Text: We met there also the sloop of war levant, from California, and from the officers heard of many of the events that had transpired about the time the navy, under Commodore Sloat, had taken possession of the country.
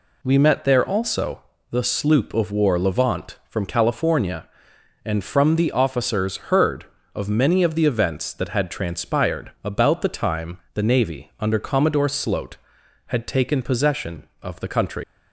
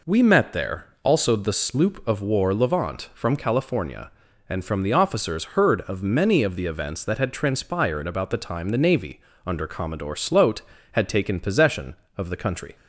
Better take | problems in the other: second | pauses between "also" and "the"; slight; at 1.4 s; 0.30 s long // leaves "country" unfinished; at 15.0 s; 95 ms

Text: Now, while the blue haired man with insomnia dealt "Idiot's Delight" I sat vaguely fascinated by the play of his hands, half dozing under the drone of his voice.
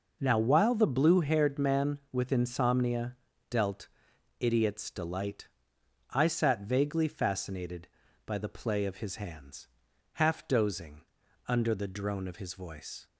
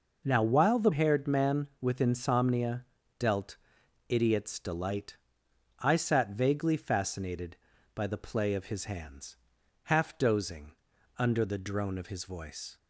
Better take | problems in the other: first | skips "blue"; at 0.9 s // pauses between "insomnia" and "dealt"; slight; at 2.8 s; 0.36 s long; slight in the first // pauses between "dealt" and "Idiot's"; noticeable; at 3.5 s; 0.54 s long; noticeable in the first // pauses between "Delight" and "I"; noticeable; at 5.1 s; 0.64 s long; noticeable in the first // pauses between "dozing" and "under"; noticeable; at 10.7 s; 0.46 s long; noticeable in the first

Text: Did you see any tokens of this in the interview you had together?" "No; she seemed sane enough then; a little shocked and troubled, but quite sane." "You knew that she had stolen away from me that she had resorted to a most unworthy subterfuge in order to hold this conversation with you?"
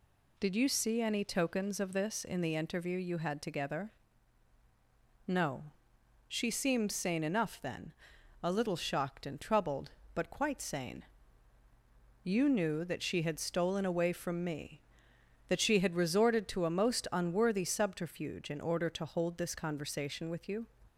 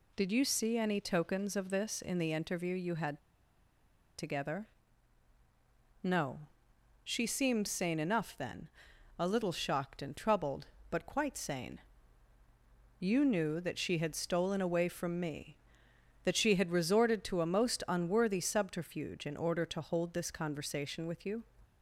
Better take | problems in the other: first | pauses between "had" and "together"; at 3.1 s; 1.0 s long

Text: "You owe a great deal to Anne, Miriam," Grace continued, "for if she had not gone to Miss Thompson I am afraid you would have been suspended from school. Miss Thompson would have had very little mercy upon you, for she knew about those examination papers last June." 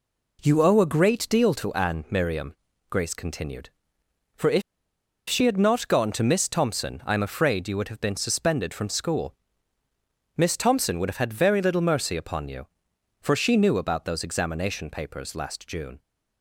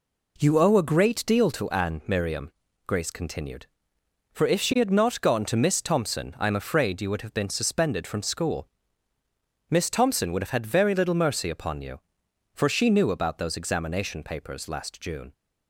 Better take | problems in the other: second | pauses between "if" and "she"; noticeable; at 4.6 s; 0.67 s long

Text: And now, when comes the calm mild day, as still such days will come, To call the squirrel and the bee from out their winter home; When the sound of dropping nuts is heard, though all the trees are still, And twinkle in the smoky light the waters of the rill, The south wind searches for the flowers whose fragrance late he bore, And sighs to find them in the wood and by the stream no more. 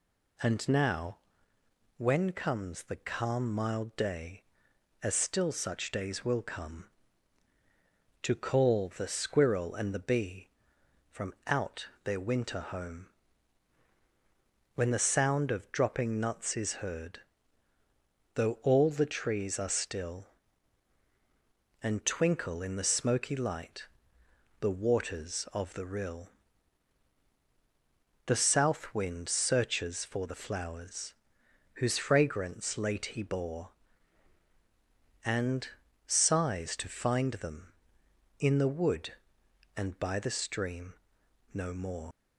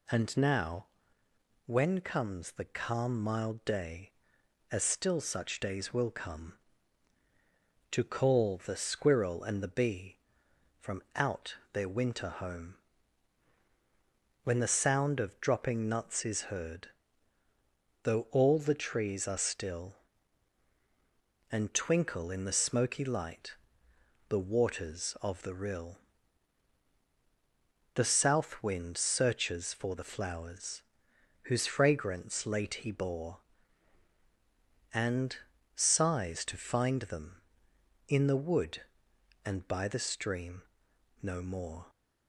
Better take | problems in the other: second | pauses between "out" and "their"; slight; at 11.8 s; 0.16 s long; slight in the second // pauses between "light" and "the"; noticeable; at 23.8 s; 0.72 s long; noticeable in the second // pauses between "flowers" and "whose"; noticeable; at 31.1 s; 0.62 s long; noticeable in the second // pauses between "And" and "sighs"; at 35.6 s; 0.40 s long; also in the second // pauses between "stream" and "no"; noticeable; at 40.9 s; 0.58 s long; noticeable in the second // leaves "more" unfinished; at 42.1 s; 100 ms

